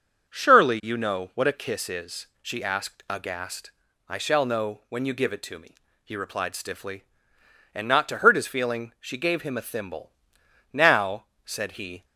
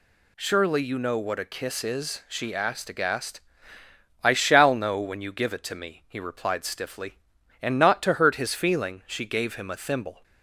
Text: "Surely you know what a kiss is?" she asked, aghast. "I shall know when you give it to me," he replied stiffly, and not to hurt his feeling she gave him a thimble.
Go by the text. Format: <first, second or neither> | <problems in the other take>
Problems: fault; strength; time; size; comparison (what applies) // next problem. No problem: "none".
second | starts louder than the rest; until 1.3 s; 6.5 dB // goes on to say "Now said he"; from 10.7 s on; 1.3 s long